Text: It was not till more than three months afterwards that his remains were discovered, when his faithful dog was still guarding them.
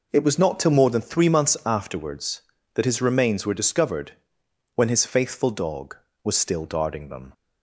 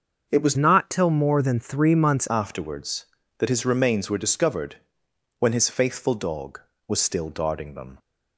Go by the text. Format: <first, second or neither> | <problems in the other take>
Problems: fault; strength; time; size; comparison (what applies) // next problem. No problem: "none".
first | starts louder than the rest; until 1.3 s; 6.5 dB // changes voice from "not" to "months"; from 0.5 to 2.2 s; 1.7 s long